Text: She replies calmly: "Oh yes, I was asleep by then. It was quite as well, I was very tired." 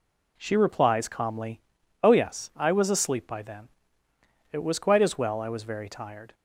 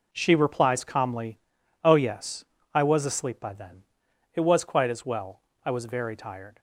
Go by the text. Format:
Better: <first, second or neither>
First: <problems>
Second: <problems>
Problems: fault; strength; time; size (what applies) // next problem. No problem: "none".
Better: neither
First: none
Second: none